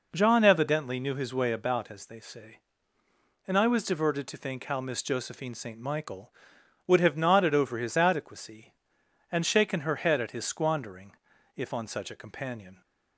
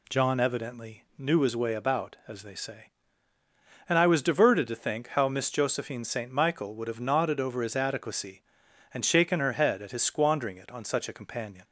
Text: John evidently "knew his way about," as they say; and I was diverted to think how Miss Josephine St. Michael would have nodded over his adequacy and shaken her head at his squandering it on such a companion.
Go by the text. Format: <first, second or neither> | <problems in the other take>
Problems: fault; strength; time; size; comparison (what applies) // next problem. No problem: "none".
second | says "if" for "it"; at 11.5 s